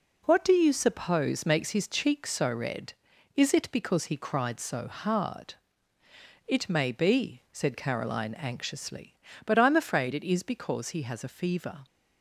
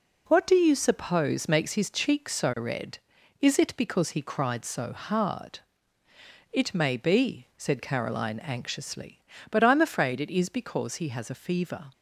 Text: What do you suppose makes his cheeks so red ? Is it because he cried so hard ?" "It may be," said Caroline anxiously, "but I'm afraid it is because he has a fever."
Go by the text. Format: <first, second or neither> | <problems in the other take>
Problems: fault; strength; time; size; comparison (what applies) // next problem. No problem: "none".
neither | none